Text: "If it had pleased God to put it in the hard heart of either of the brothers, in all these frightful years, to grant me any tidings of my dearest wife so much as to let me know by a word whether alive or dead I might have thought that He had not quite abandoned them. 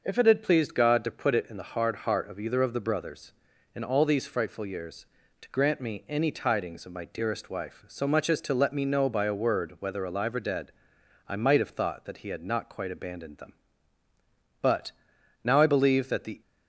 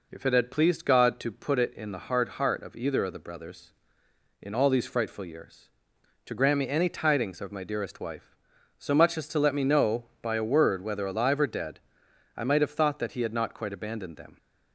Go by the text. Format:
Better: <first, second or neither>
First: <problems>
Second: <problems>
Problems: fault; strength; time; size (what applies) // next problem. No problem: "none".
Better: second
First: starts louder than the rest; noticeable; until 1.0 s; 6 dB // pauses between "dead" and "I"; noticeable; at 10.7 s; 0.56 s long // goes on to say "But now I believe that the"; strong; from 14.6 s on; 1.8 s long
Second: pauses between "dead" and "I"; noticeable; at 11.7 s; 0.56 s long